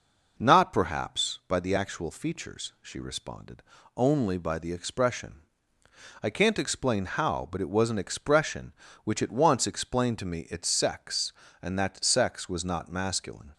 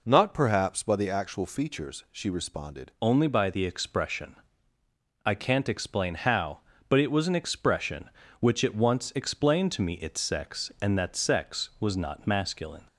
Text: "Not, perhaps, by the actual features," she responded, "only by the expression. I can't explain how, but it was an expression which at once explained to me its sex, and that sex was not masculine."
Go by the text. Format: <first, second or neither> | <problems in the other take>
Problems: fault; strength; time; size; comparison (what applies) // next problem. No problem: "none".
first | changes voice at "only"; from 2.9 s on; 9.9 s long